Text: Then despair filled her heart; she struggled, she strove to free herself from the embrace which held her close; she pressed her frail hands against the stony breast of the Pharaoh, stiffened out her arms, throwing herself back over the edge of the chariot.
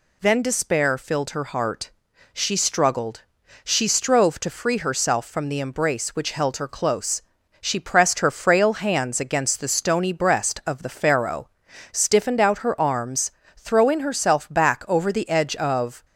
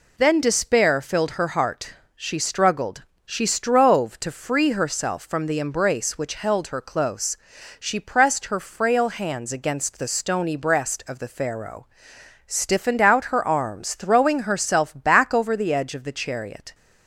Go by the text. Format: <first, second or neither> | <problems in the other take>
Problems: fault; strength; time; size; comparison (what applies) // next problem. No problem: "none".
second | stops before "the chariot"; at 16.0 s